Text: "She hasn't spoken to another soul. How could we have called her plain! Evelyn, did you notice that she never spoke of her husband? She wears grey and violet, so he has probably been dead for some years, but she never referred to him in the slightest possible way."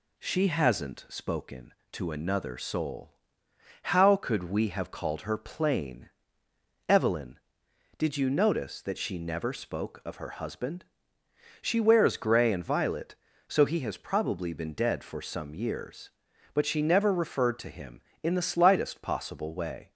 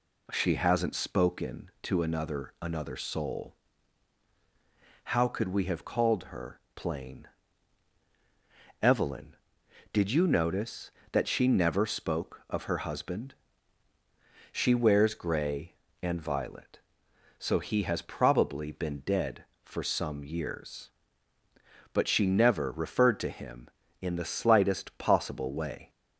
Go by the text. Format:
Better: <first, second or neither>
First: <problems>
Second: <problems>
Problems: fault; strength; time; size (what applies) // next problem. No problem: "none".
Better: first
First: none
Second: says "another" twice; at 2.5 s